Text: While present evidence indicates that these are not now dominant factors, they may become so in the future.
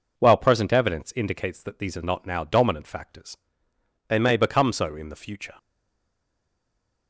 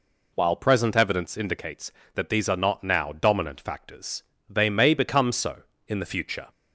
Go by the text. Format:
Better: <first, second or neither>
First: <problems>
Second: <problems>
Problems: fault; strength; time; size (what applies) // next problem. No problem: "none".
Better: second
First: stays silent after the last word; noticeable; from 5.5 s on; 1.5 s long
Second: none